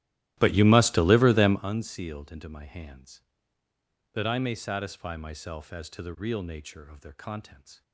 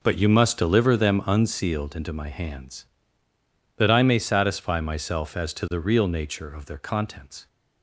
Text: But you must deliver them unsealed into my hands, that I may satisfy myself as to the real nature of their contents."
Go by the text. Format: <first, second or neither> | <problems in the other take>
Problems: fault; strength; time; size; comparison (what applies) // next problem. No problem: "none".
second | starts louder than the rest; strong; until 1.6 s; 15 dB